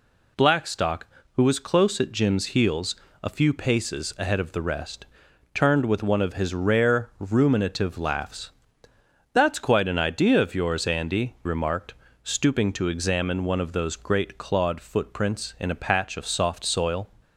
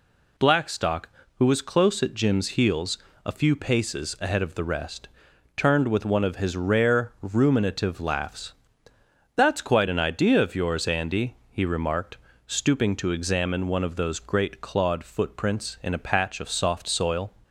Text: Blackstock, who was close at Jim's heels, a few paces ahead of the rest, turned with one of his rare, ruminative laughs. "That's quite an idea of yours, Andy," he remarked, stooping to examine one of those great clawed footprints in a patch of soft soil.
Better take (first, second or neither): second